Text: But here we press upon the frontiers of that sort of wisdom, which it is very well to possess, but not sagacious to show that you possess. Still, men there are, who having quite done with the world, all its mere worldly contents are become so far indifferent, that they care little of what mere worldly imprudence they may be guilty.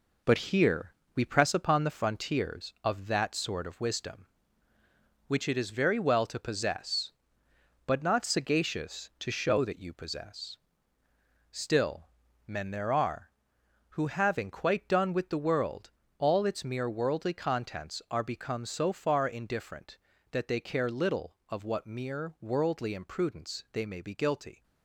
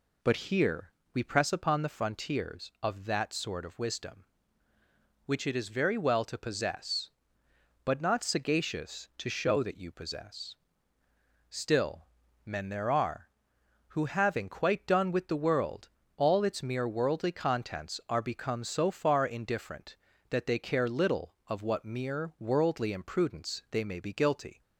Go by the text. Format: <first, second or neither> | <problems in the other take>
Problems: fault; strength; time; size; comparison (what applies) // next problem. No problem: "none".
second | gets quieter; noticeable; throughout; 6 dB // pauses between "here" and "we"; slight; at 0.9 s; 0.22 s long; slight in the second